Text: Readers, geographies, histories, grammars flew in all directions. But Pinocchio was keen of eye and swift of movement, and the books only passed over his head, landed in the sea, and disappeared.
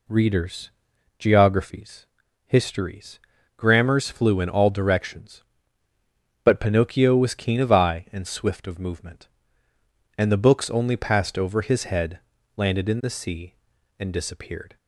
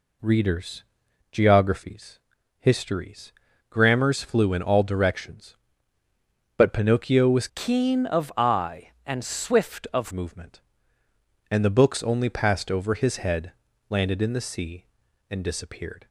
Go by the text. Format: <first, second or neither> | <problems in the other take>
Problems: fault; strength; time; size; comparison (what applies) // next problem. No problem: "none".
first | changes voice from "keen" to "of"; from 7.5 to 10.1 s; 2.6 s long